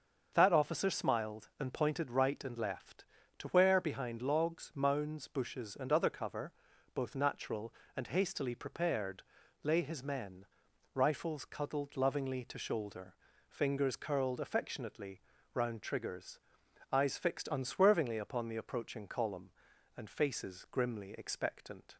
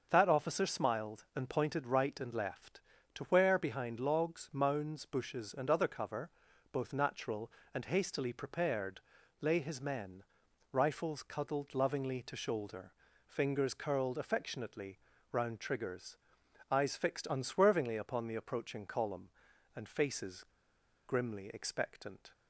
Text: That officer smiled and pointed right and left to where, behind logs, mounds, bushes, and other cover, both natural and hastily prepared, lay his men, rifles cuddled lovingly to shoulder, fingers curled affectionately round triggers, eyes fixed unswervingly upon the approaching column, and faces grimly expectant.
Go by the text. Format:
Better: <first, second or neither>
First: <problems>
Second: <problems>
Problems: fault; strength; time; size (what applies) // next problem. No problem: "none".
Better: first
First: starts louder than the rest; until 1.3 s; 6.5 dB // pauses between "affectionately" and "round"; slight; at 15.2 s; 0.32 s long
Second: starts louder than the rest; until 1.1 s; 6.5 dB // pauses between "affectionately" and "round"; slight; at 14.9 s; 0.32 s long // pauses between "faces" and "grimly"; noticeable; at 20.4 s; 0.62 s long